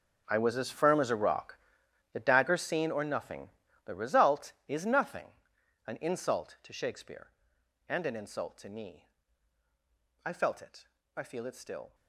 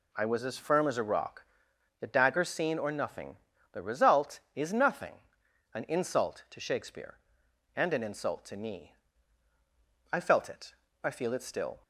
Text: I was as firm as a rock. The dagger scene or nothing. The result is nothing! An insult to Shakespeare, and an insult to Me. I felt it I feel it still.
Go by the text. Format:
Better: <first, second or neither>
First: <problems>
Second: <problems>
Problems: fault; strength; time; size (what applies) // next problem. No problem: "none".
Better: second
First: gets quieter; strong; throughout; 16 dB // pauses between "it" and "I"; slight; at 10.8 s; 0.28 s long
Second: pauses between "it" and "I"; slight; at 10.7 s; 0.28 s long